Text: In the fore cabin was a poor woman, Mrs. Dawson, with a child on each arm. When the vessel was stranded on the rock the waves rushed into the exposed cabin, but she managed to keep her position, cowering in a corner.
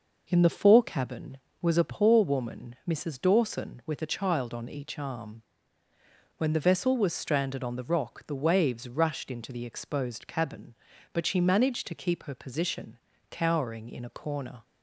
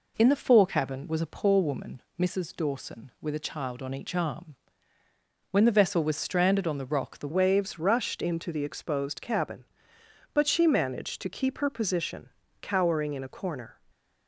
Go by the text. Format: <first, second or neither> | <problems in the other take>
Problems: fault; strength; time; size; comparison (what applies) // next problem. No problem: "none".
first | changes voice at "waves"; from 7.3 s on; 6.4 s long // stays silent after the last word; slight; from 13.7 s on; 0.5 s long